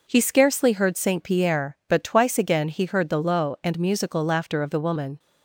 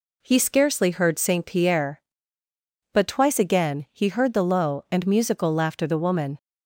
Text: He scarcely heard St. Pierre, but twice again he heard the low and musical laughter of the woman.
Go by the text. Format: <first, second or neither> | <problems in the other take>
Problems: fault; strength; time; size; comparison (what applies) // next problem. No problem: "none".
first | skips "of"; at 5.8 s